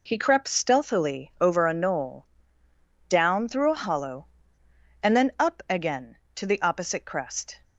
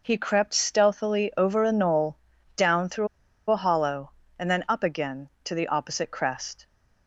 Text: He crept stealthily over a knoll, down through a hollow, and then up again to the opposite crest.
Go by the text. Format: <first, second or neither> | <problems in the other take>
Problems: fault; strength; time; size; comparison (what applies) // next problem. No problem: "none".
first | pauses between "through" and "a"; at 3.0 s; 0.43 s long